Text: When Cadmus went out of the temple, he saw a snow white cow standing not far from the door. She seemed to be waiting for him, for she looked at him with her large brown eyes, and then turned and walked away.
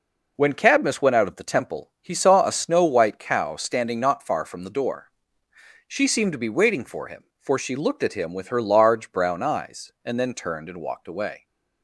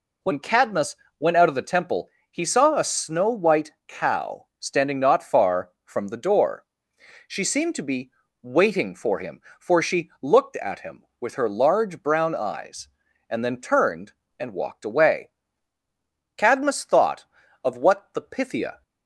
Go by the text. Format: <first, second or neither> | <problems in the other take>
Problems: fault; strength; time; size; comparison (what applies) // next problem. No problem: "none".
first | pauses between "Cadmus" and "went"; slight; at 0.9 s; 0.24 s long // pauses between "white" and "cow"; slight; at 3.7 s; 0.16 s long // pauses between "be" and "waiting"; slight; at 8.1 s; 0.32 s long // goes on to say "Cadmus thought of what the Pythia"; strong; from 16.3 s on; 2.4 s long